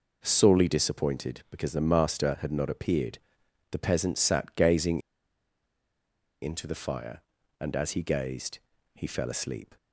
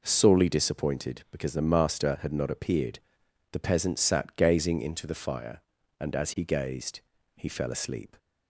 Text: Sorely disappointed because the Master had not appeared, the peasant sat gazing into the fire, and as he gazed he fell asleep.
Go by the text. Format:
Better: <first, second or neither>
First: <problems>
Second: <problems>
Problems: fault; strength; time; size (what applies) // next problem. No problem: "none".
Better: second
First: pauses between "gazing" and "into"; strong; at 5.0 s; 1.4 s long // pauses between "gazed" and "he"; slight; at 8.5 s; 0.36 s long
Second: pauses between "gazed" and "he"; slight; at 6.9 s; 0.36 s long